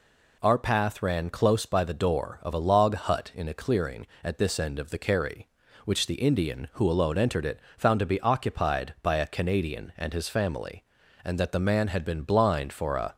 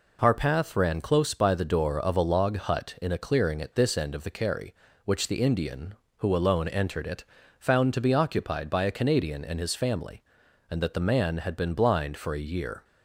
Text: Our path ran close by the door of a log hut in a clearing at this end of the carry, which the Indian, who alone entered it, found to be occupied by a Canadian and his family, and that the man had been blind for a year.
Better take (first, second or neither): second